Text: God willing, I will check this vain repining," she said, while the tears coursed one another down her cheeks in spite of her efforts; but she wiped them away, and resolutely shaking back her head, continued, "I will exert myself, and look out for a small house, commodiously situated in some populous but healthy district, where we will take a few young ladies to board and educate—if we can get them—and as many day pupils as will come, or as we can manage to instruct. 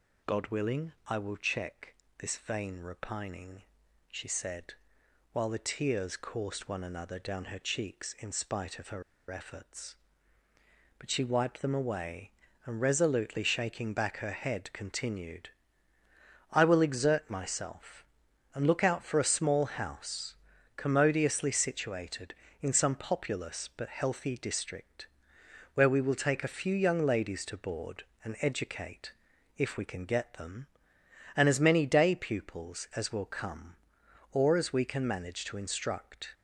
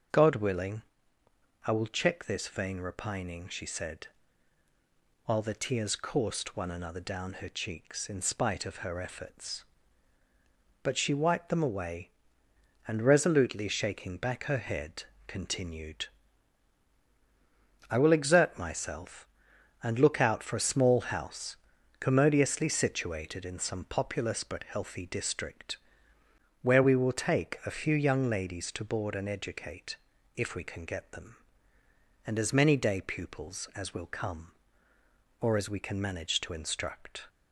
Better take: second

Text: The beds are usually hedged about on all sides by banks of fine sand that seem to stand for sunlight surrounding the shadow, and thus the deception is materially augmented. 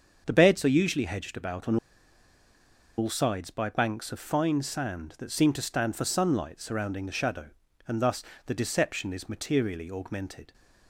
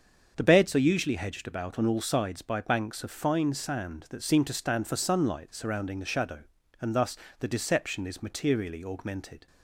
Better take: second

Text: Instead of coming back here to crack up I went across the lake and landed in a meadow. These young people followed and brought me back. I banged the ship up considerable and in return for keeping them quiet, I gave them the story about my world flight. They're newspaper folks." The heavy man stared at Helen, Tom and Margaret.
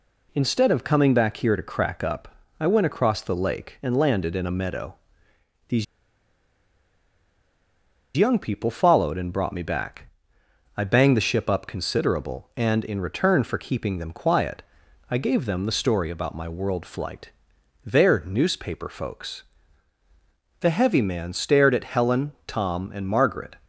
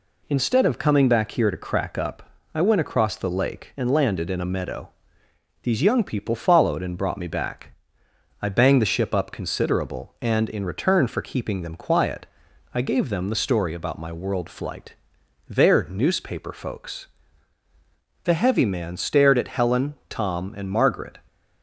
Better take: second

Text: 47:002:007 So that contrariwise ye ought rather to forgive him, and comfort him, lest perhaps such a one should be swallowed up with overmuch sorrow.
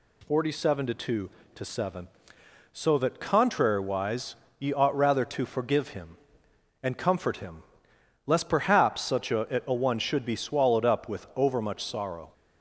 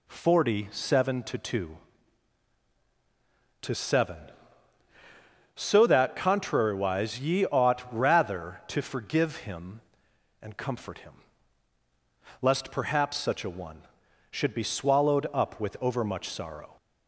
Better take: second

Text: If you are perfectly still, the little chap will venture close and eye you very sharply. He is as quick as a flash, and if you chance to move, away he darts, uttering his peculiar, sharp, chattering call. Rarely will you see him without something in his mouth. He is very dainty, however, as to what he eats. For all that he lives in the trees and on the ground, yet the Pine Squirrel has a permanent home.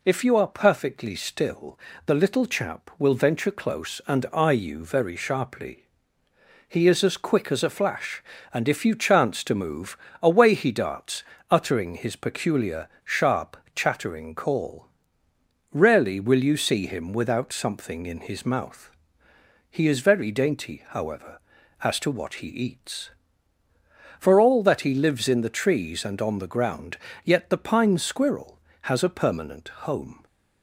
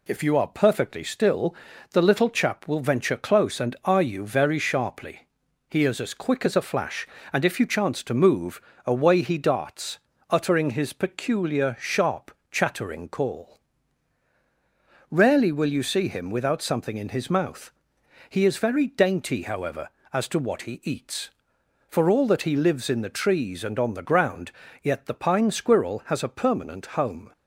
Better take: neither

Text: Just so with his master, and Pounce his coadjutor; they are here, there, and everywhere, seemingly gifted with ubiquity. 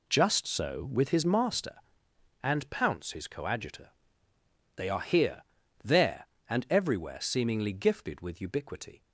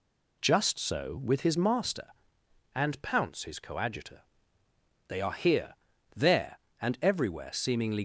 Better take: first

